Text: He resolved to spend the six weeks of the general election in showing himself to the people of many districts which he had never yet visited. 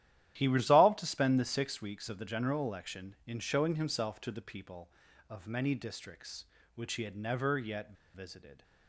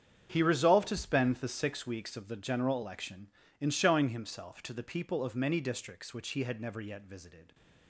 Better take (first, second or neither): second